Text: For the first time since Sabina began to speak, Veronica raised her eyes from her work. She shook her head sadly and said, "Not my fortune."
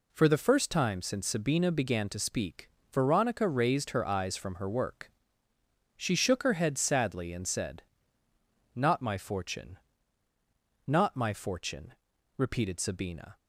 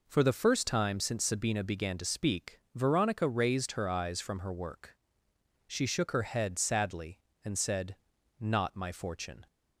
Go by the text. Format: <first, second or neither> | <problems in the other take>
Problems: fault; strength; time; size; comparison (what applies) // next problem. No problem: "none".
second | goes on to say "Not my fortune repeated Sabina"; strong; from 10.8 s on; 2.5 s long